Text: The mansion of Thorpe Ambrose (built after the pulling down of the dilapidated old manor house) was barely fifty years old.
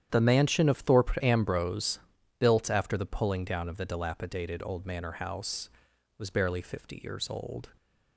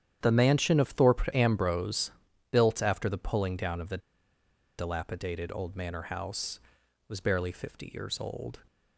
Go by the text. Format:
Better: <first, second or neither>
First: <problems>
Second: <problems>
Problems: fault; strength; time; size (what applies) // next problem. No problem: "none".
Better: first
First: starts louder than the rest; strong; until 1.1 s; 9.5 dB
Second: starts louder than the rest; strong; until 1.2 s; 9.5 dB // pauses between "the" and "dilapidated"; noticeable; at 3.9 s; 0.80 s long